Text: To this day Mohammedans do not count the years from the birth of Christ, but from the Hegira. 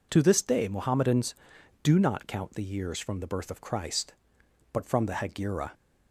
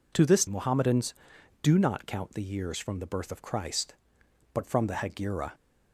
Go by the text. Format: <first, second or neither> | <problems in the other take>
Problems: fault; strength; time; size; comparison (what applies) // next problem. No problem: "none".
first | skips "day"; at 0.4 s